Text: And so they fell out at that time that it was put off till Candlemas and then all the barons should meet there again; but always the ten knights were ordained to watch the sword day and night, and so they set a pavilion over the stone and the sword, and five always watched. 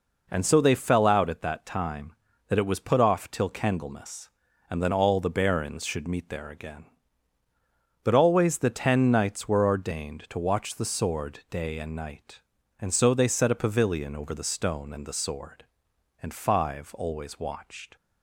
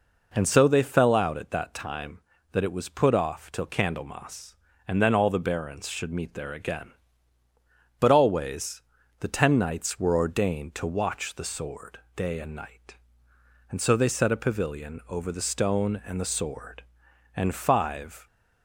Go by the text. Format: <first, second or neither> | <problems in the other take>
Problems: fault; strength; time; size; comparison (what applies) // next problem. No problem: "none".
first | pauses between "always" and "the"; at 8.8 s; 0.40 s long // pauses between "sword" and "day"; slight; at 11.9 s; 0.18 s long // stops before "always watched"; at 18.2 s